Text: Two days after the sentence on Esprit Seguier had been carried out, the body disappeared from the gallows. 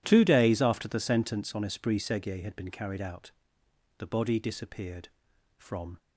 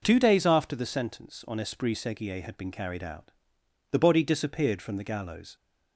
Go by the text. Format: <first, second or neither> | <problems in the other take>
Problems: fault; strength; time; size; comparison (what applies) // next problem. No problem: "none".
second | stops before "the gallows"; at 5.9 s